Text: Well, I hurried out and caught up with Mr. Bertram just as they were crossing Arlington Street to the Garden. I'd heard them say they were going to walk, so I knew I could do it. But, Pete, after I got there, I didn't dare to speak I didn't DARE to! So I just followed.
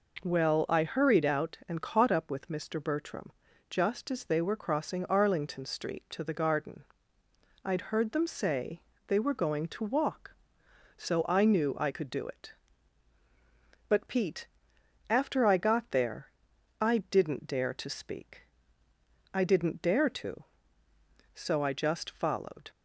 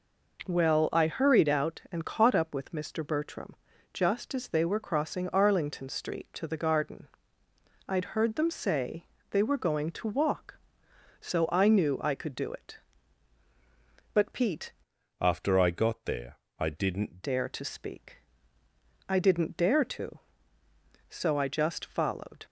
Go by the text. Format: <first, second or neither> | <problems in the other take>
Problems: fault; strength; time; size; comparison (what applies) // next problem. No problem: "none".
first | pauses between "Bertram" and "just"; at 3.5 s; 0.38 s long; also in the first // pauses between "say" and "they"; slight; at 9.0 s; 0.28 s long; slight in the first // changes voice from "after" to "didn't"; from 15.1 to 17.2 s; 2.1 s long // pauses between "speak" and "I"; noticeable; at 18.1 s; 0.94 s long; noticeable in the first